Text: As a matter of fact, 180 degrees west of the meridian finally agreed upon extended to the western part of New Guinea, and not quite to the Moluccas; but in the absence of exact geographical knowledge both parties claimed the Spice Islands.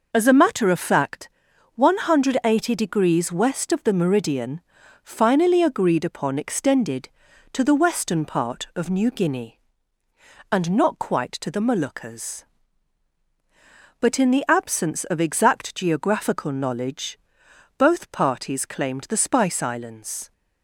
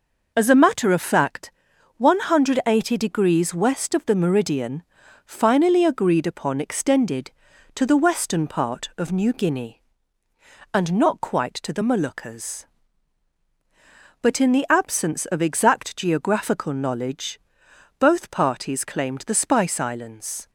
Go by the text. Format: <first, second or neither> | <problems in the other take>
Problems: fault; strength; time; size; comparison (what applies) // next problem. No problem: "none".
neither | pauses between "meridian" and "finally"; the same in both // pauses between "knowledge" and "both"; noticeable; the same in both